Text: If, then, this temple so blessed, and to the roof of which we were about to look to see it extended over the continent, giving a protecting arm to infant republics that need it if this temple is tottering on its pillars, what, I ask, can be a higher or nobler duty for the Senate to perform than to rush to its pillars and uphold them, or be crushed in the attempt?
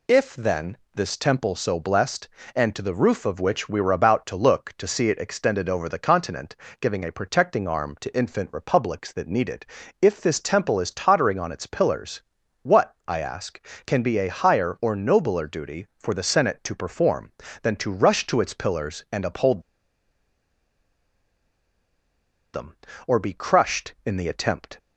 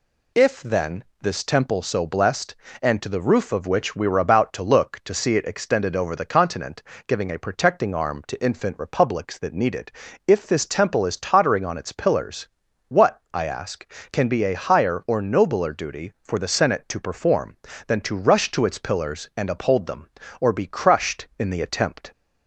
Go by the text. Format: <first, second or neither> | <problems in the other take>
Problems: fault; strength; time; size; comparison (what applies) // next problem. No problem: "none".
second | pauses between "it" and "if"; at 9.6 s; 0.38 s long; also in the second // pauses between "uphold" and "them"; strong; at 19.6 s; 2.9 s long